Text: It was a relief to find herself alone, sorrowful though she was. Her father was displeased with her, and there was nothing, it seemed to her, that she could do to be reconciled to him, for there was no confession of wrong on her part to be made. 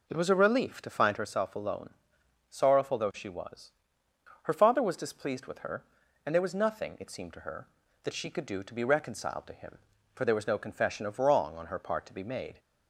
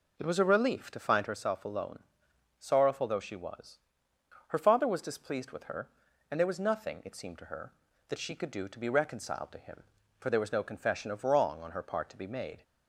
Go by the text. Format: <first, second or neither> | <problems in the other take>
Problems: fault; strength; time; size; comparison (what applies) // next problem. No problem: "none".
neither | none